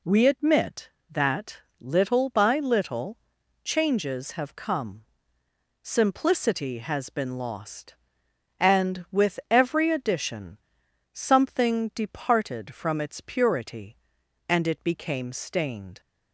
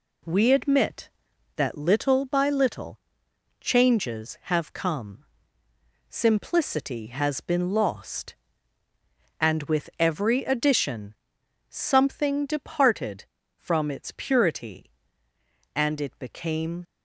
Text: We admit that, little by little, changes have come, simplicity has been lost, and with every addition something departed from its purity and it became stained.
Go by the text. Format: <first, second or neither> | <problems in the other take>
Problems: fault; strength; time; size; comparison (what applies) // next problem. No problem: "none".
first | pauses between "addition" and "something"; noticeable; at 11.1 s; 0.54 s long; noticeable in the first // stops before "stained"; at 16.8 s